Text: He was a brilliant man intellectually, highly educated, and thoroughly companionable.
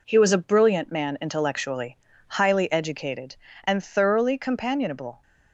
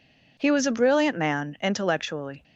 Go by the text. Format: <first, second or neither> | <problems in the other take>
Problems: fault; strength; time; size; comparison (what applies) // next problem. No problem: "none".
first | stops before "highly educated and thoroughly companionable"; at 2.4 s